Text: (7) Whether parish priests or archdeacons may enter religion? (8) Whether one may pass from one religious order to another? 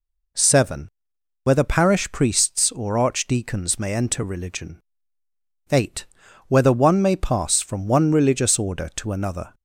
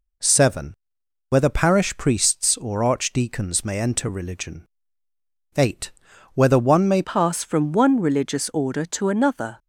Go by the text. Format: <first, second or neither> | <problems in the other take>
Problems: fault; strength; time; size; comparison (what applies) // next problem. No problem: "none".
first | changes voice at "pass"; from 7.0 s on; 2.5 s long